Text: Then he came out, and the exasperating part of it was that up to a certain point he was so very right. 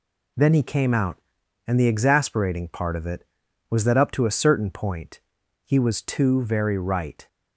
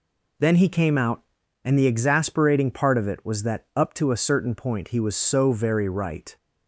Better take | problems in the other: second | pauses between "point" and "he"; noticeable; at 5.1 s; 0.46 s long // says "too" for "so"; at 6.0 s

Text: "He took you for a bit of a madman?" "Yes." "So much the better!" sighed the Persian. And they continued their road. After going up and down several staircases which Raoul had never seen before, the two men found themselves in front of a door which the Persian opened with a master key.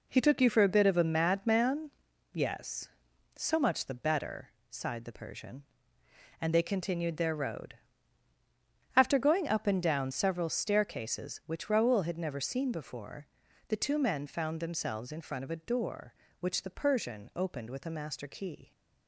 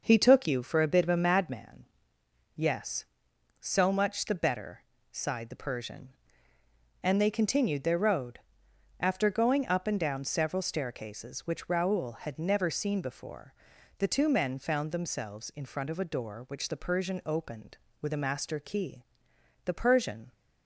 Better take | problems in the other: first | goes on to say "The Persian"; noticeable; from 19.6 s on; 0.66 s long

